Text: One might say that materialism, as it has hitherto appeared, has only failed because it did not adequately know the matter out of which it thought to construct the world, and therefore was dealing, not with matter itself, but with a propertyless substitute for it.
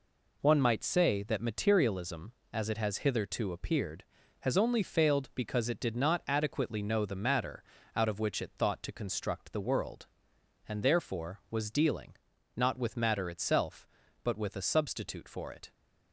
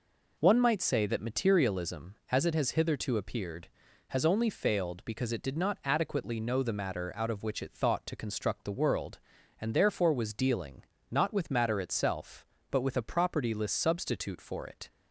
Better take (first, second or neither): second